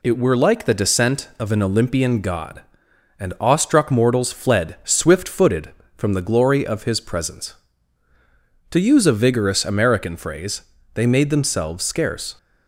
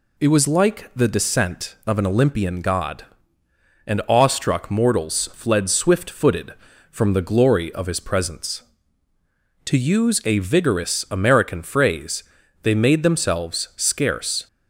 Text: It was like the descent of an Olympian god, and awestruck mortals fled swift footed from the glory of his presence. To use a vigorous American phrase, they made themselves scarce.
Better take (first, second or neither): second